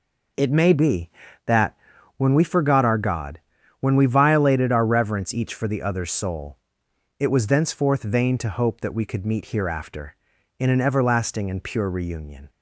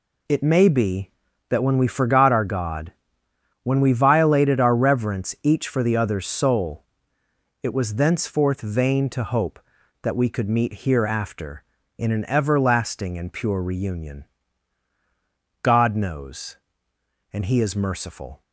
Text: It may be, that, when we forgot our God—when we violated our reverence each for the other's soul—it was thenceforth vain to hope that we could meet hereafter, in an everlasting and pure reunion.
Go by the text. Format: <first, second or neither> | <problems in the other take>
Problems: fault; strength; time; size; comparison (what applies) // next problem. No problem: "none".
first | goes on to say "God knows and He is merciful"; strong; from 15.6 s on; 2.8 s long